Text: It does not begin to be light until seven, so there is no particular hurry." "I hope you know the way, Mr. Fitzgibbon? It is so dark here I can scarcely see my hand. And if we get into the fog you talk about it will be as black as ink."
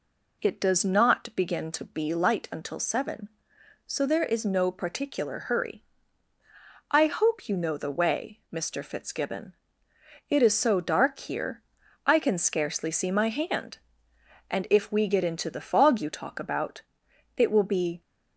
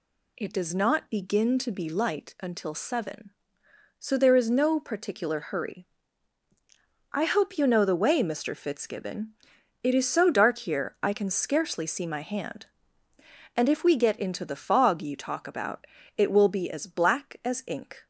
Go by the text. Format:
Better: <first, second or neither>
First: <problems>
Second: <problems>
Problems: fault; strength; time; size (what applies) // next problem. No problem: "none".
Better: second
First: pauses between "here" and "I"; noticeable; at 11.6 s; 0.46 s long // pauses between "about" and "it"; noticeable; at 16.8 s; 0.52 s long // stops before "as black as ink"; at 18.0 s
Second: pauses between "about" and "it"; slight; at 15.8 s; 0.30 s long